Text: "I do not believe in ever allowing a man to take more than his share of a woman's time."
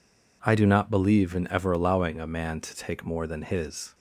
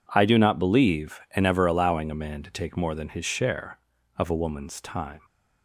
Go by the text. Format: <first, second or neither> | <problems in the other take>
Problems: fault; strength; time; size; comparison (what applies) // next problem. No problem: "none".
second | stops before "share of a woman's time"; at 3.9 s